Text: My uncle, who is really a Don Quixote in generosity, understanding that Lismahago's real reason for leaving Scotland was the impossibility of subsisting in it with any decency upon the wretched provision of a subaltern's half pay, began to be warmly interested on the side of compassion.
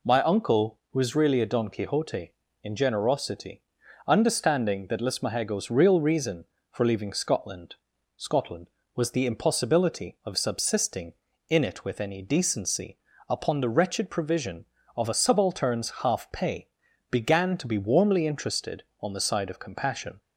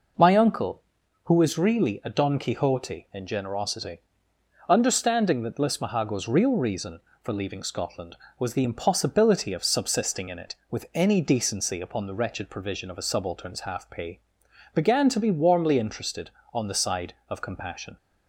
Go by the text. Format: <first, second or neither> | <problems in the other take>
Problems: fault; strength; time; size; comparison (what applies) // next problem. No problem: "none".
second | says "Scotland" twice; at 8.1 s // pauses between "decency" and "upon"; slight; at 12.9 s; 0.30 s long